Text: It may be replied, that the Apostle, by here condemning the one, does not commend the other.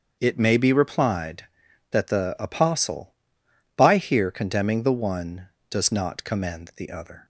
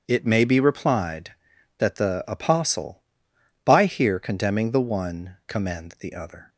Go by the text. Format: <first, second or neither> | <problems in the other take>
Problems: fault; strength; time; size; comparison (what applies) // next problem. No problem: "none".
first | starts louder than the rest; strong; until 1.0 s; 7.5 dB; also in the first // skips "does not"; at 5.4 s